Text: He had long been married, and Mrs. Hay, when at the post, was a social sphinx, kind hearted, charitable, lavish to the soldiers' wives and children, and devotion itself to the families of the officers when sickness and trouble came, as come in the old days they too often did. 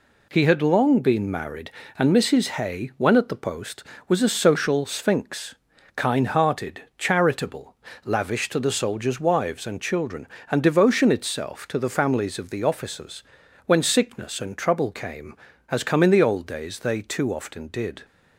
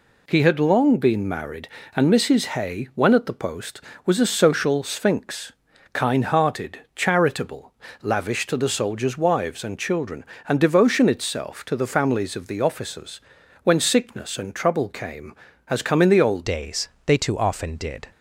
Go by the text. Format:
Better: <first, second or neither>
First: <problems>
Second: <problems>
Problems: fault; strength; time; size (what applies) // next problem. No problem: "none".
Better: first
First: pauses between "officers" and "when"; at 13.2 s; 0.42 s long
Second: pauses between "officers" and "when"; at 13.1 s; 0.42 s long // changes voice at "days"; from 16.4 s on; 1.6 s long // pauses between "days" and "they"; slight; at 16.8 s; 0.20 s long